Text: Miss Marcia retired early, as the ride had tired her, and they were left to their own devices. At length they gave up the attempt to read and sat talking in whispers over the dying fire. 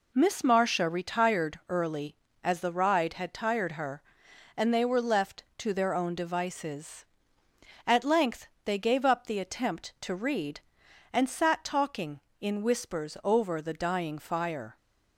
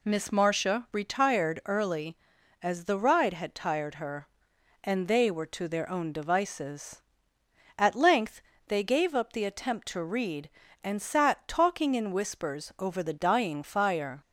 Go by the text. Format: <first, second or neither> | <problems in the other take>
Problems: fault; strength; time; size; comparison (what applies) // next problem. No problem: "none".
first | skips "left"; at 5.4 s // pauses between "length" and "they"; slight; at 8.4 s; 0.26 s long; slight in the first